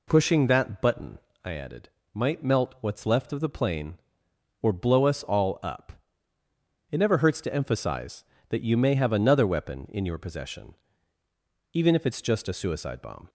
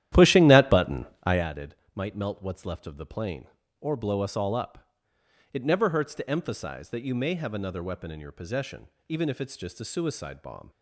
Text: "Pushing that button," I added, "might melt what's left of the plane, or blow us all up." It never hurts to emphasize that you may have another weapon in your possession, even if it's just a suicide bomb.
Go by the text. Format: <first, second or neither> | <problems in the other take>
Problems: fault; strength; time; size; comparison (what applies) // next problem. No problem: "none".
first | starts louder than the rest; strong; until 1.5 s; 12 dB